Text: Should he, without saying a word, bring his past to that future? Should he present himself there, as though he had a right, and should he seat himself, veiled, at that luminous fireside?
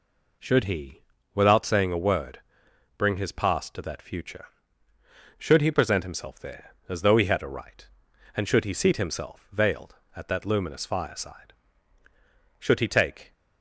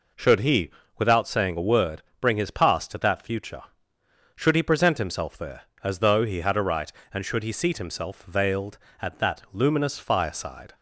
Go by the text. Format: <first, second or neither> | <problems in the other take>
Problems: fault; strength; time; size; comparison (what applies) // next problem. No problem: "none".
second | goes on to say "Should he take"; noticeable; from 12.5 s on; 0.74 s long